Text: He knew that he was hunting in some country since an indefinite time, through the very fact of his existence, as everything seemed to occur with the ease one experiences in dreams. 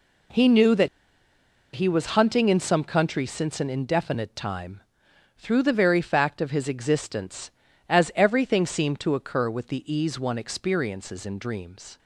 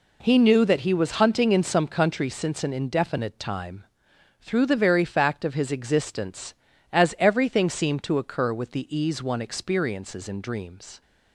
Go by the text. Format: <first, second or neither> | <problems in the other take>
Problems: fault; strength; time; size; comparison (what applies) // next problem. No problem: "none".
second | pauses between "that" and "he"; noticeable; at 0.8 s; 0.87 s long